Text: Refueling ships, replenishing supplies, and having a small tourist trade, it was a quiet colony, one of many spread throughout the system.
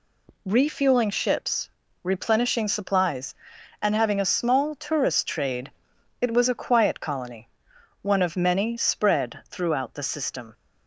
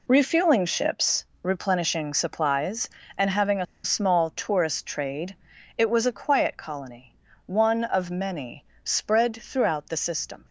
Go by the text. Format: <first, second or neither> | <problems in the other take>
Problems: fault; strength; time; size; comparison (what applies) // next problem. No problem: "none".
first | pauses between "a" and "small"; slight; at 3.6 s; 0.19 s long // pauses between "many" and "spread"; slight; at 8.6 s; 0.18 s long